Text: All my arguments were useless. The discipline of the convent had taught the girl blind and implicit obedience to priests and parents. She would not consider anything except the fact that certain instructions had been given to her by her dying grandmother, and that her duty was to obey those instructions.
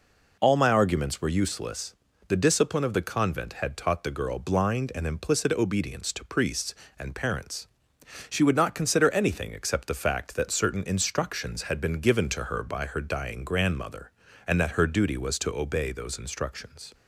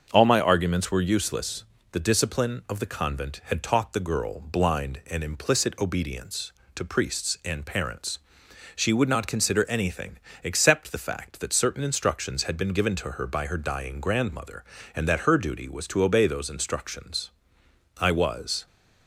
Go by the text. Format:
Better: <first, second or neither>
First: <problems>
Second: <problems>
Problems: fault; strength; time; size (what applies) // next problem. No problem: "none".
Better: first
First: none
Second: starts louder than the rest; until 1.1 s; 6.5 dB // pauses between "anything" and "except"; slight; at 10.1 s; 0.26 s long // goes on to say "I was"; noticeable; from 17.9 s on; 0.68 s long